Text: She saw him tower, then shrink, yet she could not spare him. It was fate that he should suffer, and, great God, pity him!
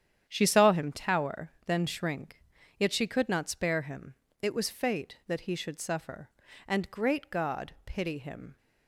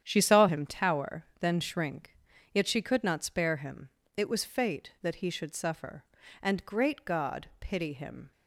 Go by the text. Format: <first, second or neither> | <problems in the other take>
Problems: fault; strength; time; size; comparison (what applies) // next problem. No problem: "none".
neither | starts louder than the rest; strong; the same in both